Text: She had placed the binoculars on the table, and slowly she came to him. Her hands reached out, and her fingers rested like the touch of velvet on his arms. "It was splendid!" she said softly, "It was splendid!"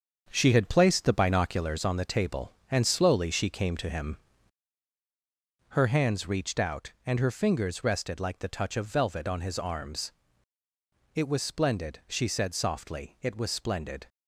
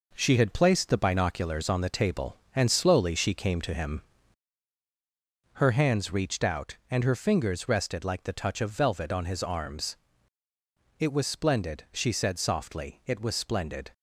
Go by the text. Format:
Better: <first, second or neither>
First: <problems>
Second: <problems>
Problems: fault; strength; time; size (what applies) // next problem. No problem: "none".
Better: second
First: starts louder than the rest; until 1.8 s; 7 dB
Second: none